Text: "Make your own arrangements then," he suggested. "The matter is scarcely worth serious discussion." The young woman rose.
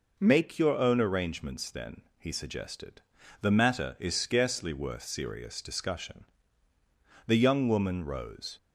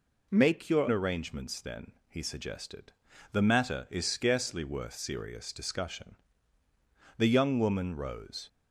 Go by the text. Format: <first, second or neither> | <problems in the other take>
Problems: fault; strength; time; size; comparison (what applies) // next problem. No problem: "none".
first | skips "own"; at 0.8 s